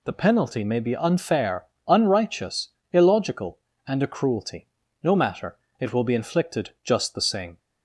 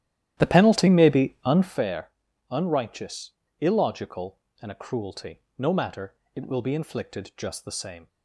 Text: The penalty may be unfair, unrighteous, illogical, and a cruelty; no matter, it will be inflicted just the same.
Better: first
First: none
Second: starts louder than the rest; strong; until 1.8 s; 12.5 dB

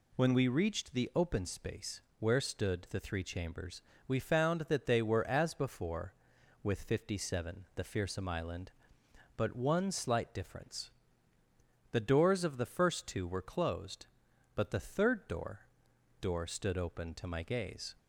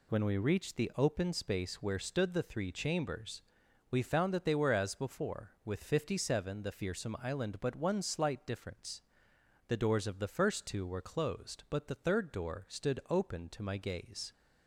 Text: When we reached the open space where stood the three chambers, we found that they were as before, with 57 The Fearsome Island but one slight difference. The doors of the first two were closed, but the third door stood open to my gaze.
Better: second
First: pauses between "space" and "where"; slight; at 2.0 s; 0.18 s long // says "door" twice; at 16.2 s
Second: none

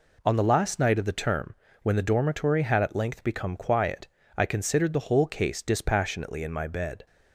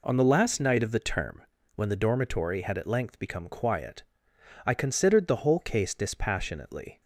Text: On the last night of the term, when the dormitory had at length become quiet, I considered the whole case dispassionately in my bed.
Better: first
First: none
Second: stops before "in my bed"; at 7.0 s

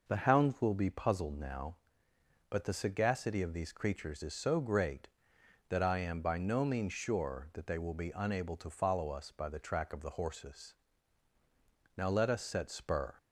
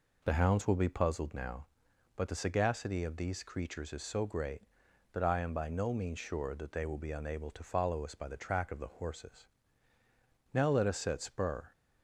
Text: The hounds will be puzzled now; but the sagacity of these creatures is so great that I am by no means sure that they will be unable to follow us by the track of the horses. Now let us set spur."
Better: neither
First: none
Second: none

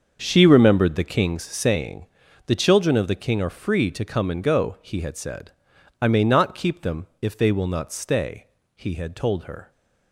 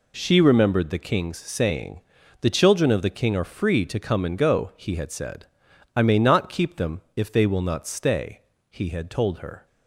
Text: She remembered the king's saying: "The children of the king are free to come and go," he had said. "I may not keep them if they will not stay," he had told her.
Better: second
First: starts louder than the rest; until 1.8 s; 6.5 dB // pauses between "them" and "if"; slight; at 7.0 s; 0.16 s long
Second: pauses between "them" and "if"; slight; at 7.0 s; 0.16 s long

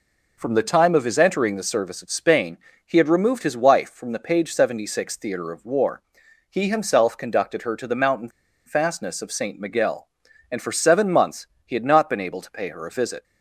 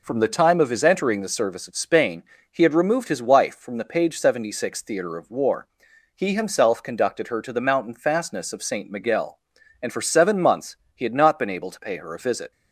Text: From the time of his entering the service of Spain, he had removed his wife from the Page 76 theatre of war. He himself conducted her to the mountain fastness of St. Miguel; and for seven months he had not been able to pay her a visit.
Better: second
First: pauses between "mountain" and "fastness"; at 8.2 s; 0.37 s long // pauses between "months" and "he"; slight; at 11.4 s; 0.22 s long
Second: pauses between "months" and "he"; slight; at 10.7 s; 0.22 s long

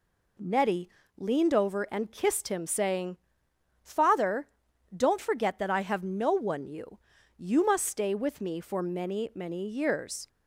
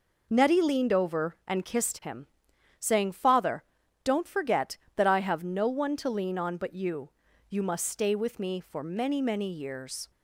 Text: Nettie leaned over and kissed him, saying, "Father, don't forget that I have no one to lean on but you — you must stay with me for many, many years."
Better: second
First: pauses between "Nettie" and "leaned"; slight; at 0.8 s; 0.28 s long // skips "to lean on but"; at 6.6 s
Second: none

